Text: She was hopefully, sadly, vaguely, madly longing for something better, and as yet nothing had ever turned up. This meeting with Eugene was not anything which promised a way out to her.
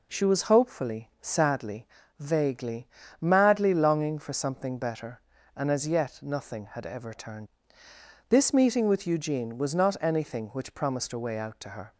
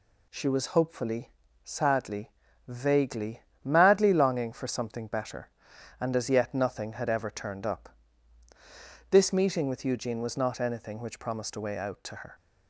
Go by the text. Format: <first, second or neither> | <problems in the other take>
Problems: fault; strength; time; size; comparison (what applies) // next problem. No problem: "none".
second | skips "up"; at 7.8 s